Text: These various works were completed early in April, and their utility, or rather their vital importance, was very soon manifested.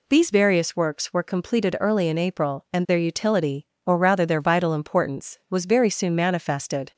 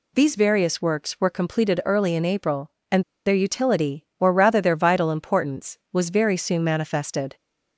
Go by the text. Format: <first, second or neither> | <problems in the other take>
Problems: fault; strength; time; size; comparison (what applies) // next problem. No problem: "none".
first | pauses between "and" and "their"; slight; at 3.0 s; 0.24 s long